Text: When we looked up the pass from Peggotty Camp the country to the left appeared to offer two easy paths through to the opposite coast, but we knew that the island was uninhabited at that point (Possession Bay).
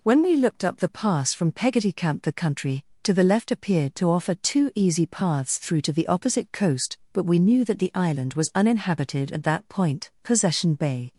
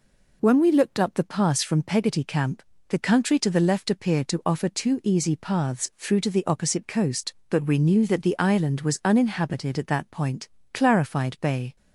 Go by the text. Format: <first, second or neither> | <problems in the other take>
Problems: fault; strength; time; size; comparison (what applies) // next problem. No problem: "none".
first | pauses between "Camp" and "the"; slight; at 2.6 s; 0.26 s long // says "Clarified" for "Possession"; at 10.7 s